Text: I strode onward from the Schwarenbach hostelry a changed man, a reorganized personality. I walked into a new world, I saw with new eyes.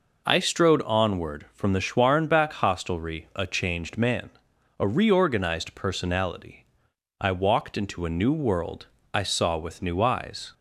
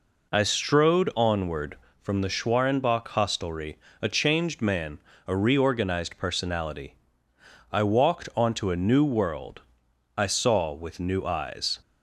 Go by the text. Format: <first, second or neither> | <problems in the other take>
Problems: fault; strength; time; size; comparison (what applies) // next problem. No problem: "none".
first | pauses between "hostelry" and "a"; slight; at 3.7 s; 0.24 s long // says "onto" for "into"; at 8.3 s